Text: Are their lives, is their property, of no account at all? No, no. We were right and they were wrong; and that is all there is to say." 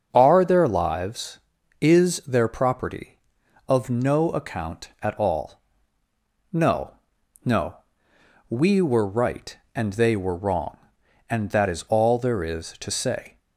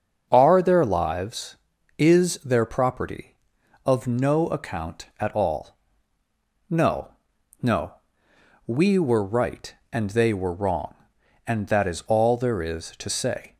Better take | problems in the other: neither | starts louder than the rest; the same in both

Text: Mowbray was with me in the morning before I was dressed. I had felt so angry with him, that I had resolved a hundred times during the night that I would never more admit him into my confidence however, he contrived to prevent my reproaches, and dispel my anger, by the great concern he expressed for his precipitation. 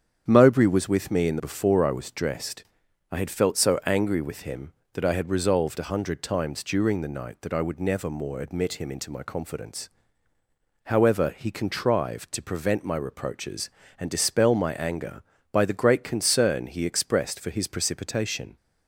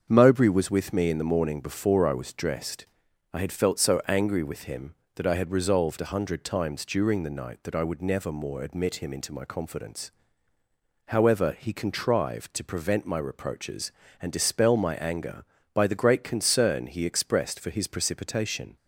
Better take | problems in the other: second | starts louder than the rest; strong; until 1.2 s; 8 dB; also in the second // skips "morning"; at 1.3 s // pauses between "confidence" and "however"; noticeable; at 9.8 s; 0.96 s long; noticeable in the second

